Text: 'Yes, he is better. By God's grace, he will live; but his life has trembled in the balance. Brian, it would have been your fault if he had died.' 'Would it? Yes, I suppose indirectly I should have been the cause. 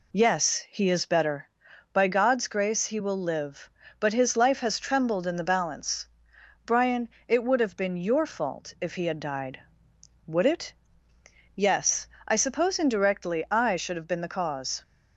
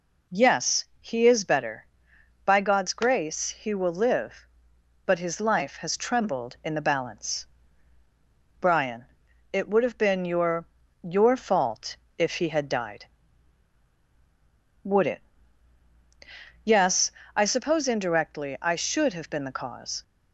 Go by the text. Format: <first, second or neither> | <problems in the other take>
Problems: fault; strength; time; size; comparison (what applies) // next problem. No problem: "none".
first | says "your" twice; at 11.0 s // pauses between "fault" and "if"; slight; at 11.9 s; 0.22 s long